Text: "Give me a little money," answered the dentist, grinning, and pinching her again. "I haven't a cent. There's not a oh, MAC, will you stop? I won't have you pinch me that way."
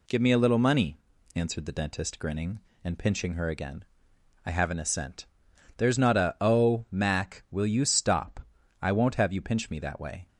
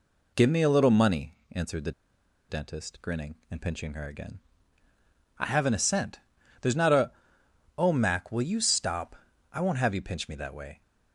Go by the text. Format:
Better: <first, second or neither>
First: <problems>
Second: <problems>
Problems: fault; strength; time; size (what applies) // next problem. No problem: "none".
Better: first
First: none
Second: pauses between "the" and "dentist"; noticeable; at 1.9 s; 0.58 s long // pauses between "a" and "oh"; noticeable; at 7.1 s; 0.66 s long